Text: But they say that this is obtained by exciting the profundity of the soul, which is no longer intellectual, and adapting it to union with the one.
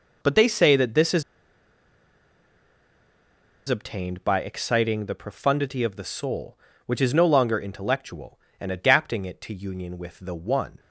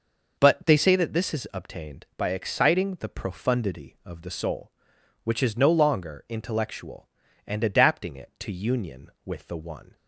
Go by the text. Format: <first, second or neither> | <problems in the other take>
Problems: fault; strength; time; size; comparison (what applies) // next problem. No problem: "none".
second | pauses between "is" and "obtained"; strong; at 1.2 s; 2.4 s long